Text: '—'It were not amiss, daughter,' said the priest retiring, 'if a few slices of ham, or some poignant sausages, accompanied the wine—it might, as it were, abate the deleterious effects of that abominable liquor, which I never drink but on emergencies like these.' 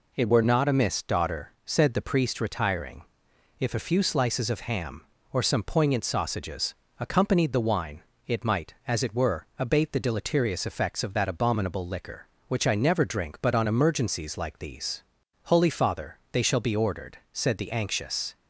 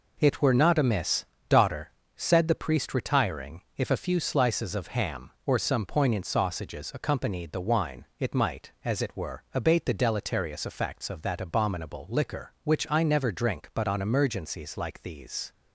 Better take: second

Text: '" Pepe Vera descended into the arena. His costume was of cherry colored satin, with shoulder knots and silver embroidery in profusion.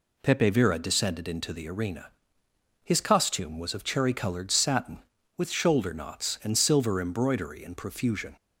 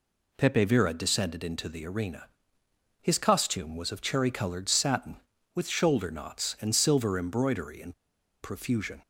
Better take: first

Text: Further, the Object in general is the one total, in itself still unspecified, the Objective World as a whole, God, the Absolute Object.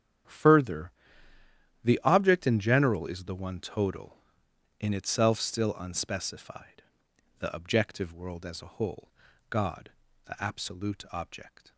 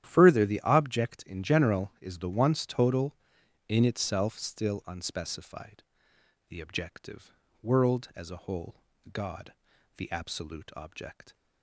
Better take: first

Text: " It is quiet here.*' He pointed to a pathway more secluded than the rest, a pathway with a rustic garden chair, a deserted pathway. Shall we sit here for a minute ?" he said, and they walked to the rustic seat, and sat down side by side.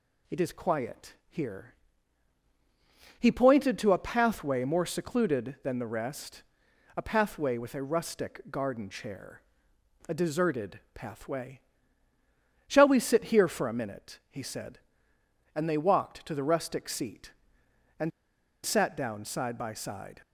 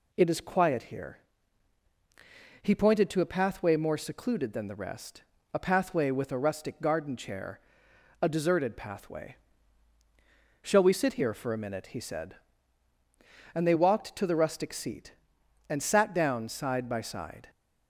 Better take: second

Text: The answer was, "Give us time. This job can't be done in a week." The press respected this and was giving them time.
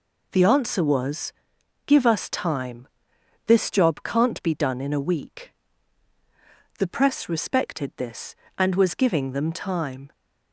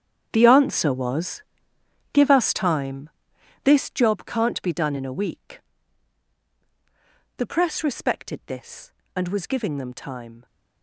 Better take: first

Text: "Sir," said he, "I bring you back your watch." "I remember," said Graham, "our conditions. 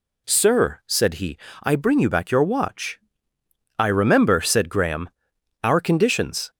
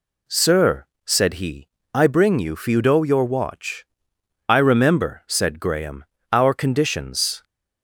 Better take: first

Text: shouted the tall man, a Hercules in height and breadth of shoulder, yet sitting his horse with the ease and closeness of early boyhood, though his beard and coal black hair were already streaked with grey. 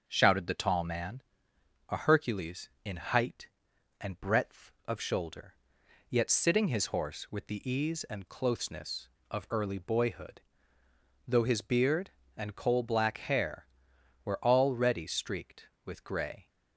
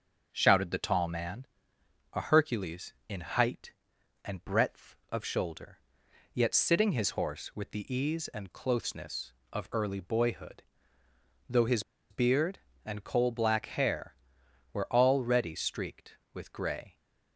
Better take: first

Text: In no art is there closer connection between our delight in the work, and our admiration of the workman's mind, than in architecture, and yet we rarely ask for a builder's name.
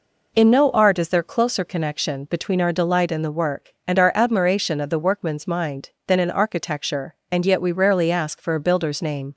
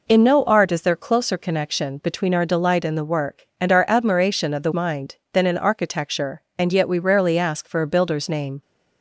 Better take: first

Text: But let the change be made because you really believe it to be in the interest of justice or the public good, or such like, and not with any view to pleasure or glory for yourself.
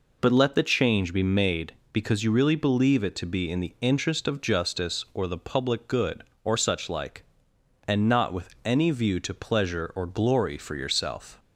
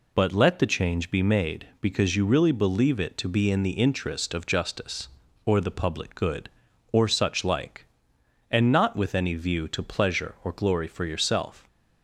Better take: neither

